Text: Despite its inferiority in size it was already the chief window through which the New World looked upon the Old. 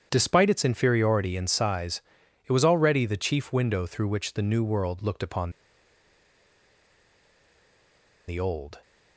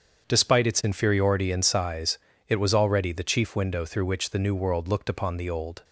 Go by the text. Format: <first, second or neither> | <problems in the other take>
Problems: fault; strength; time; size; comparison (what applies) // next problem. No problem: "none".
second | starts louder than the rest; strong; until 1.1 s; 8.5 dB; strong in the second // pauses between "size" and "it"; at 2.0 s; 0.42 s long; slight in the second // pauses between "upon" and "the"; strong; at 5.5 s; 2.7 s long